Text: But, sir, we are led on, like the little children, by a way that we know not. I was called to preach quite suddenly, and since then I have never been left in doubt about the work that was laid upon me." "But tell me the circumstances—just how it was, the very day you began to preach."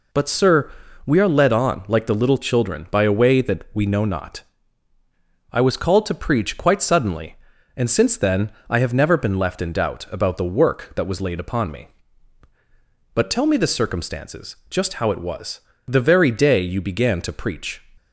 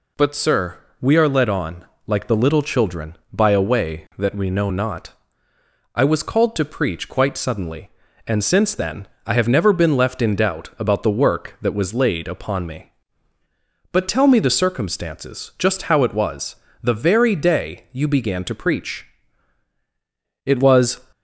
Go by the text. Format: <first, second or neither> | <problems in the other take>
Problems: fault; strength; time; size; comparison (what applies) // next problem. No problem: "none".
first | pauses between "then" and "I"; slight; at 9.0 s; 0.18 s long; slight in the first // goes on to say "It was"; from 20.4 s on; 0.56 s long